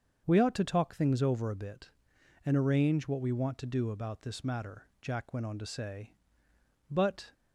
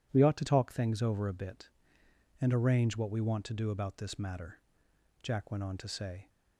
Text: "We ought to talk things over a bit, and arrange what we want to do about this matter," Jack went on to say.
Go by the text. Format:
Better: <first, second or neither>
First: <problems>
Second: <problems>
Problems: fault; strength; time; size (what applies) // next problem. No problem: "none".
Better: second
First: starts louder than the rest; until 1.2 s; 7 dB // goes on to say "But"; slight; from 6.8 s on; 0.44 s long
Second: none